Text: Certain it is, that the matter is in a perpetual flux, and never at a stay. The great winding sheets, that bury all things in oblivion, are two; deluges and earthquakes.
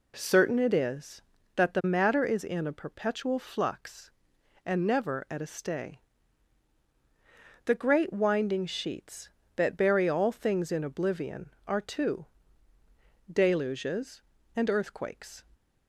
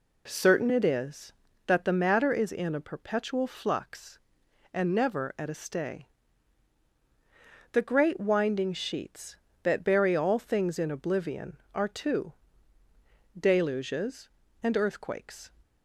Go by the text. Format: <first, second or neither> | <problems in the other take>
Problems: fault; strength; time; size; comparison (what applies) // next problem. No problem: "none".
neither | none